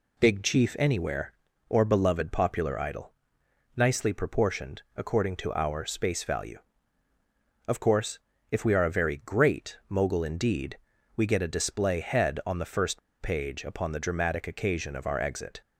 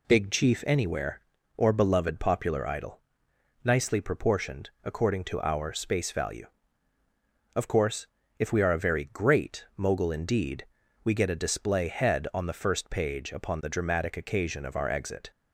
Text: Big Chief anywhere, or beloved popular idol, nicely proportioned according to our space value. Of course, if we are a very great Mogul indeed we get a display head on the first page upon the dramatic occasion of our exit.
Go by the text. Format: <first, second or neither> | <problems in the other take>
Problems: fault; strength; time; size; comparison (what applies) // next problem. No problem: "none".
second | pauses between "indeed" and "we"; slight; at 10.7 s; 0.36 s long; slight in the second // pauses between "first" and "page"; slight; at 13.0 s; 0.22 s long